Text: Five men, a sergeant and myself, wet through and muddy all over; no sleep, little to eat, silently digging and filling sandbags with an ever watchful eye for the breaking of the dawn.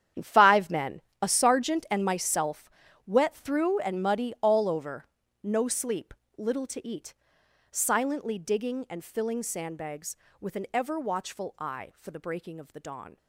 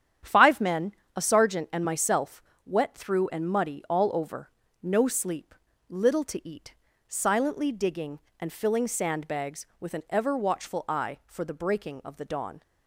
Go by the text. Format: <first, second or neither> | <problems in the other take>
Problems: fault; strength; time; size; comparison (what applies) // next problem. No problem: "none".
second | gets quieter; strong; throughout; 14 dB // starts louder than the rest; strong; until 1.4 s; 9.5 dB; strong in the second